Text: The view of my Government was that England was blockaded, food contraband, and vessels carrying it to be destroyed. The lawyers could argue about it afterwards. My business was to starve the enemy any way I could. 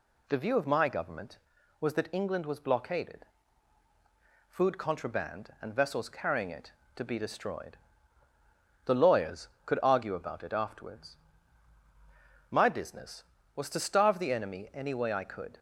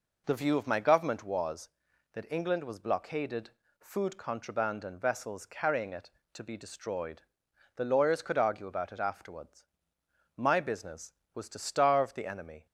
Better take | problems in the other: first | stops before "any way I could"; at 12.6 s

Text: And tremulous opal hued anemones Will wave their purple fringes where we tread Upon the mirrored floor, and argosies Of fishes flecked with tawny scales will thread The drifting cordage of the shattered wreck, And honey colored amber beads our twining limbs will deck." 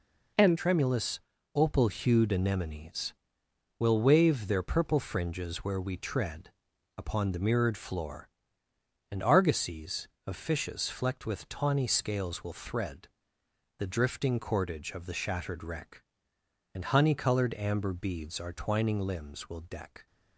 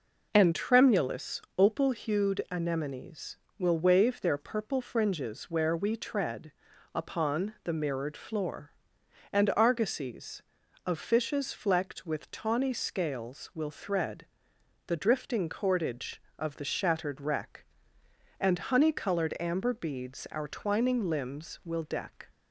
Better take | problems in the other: second | changes voice at "tremulous"; from 0.5 s on; 19.5 s long // pauses between "tremulous" and "opal"; slight; at 1.1 s; 0.34 s long; slight in the second // pauses between "tread" and "Upon"; noticeable; at 6.5 s; 0.46 s long; also in the second // pauses between "thread" and "The"; noticeable; at 13.0 s; 0.70 s long; noticeable in the second

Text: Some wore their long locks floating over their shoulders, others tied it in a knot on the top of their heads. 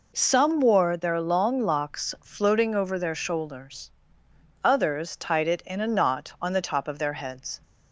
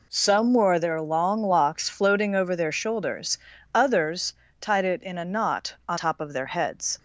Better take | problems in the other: first | pauses between "others" and "tied"; slight; at 4.3 s; 0.26 s long // skips "the"; at 5.9 s

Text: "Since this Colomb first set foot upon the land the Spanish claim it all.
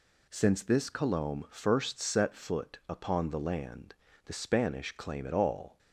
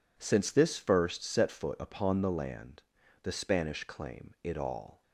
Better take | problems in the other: first | skips "Colomb"; at 0.7 s // pauses between "land" and "the"; at 2.8 s; 0.42 s long; slight in the first

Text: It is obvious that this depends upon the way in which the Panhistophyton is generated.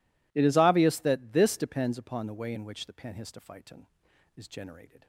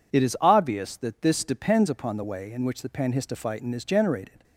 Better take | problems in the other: neither | none

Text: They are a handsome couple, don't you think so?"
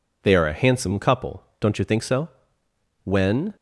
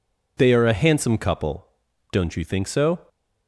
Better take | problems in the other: second | goes on to say "When"; from 3.0 s on; 0.52 s long

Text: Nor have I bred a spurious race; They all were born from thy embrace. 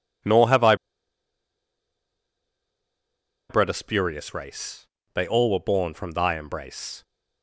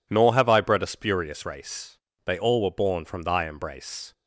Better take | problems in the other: second | pauses between "I" and "bred"; strong; at 0.7 s; 2.7 s long

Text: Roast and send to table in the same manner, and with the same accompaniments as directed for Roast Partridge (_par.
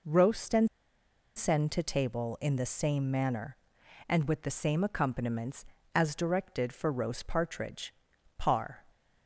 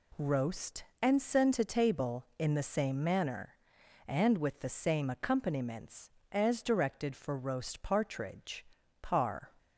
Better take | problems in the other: second | pauses between "and" and "send"; noticeable; at 0.6 s; 0.68 s long

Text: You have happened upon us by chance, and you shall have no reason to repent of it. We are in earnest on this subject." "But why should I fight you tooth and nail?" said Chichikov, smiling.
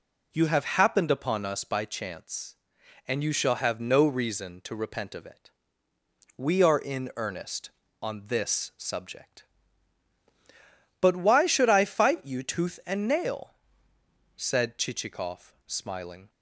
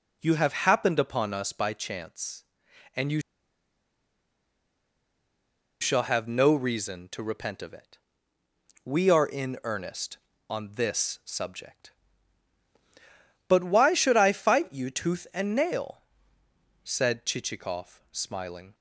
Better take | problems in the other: first | pauses between "you" and "shall"; strong; at 3.1 s; 2.6 s long

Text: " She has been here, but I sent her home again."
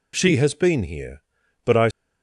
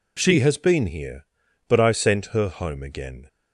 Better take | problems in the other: second | stops before "sent her home again"; at 1.9 s

